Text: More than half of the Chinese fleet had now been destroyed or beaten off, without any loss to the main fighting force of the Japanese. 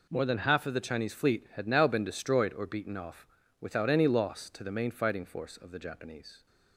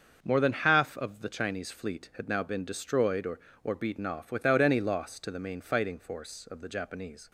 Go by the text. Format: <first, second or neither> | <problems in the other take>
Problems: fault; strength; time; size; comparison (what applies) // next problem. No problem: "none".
first | starts louder than the rest; until 1.2 s; 6.5 dB // says "or" twice; at 3.6 s